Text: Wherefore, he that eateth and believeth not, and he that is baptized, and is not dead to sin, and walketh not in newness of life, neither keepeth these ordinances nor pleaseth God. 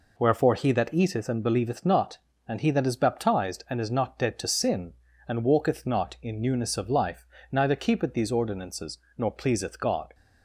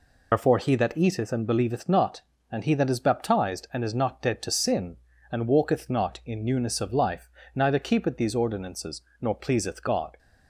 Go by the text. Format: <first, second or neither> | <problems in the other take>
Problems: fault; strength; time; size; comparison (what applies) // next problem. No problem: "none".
first | loses the start of "Wherefore"; at 0.3 s; 100 ms // pauses between "ordinances" and "nor"; slight; at 9.0 s; 0.20 s long; slight in the first